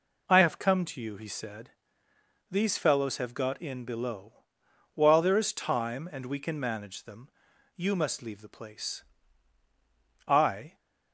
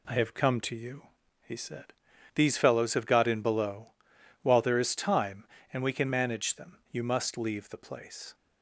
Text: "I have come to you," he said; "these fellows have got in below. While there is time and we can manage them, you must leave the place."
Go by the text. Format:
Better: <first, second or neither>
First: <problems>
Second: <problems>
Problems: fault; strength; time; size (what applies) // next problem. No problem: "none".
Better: second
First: goes on to say "I"; from 10.2 s on; 0.50 s long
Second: none